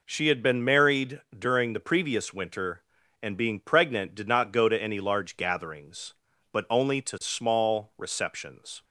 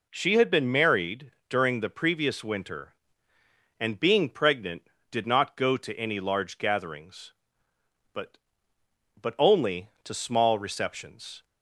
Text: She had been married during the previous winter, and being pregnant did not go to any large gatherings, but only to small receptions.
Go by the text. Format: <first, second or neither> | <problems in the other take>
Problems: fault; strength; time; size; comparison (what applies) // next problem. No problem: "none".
first | pauses between "married" and "during"; slight; at 1.3 s; 0.18 s long; slight in the first // says "but" twice; at 9.1 s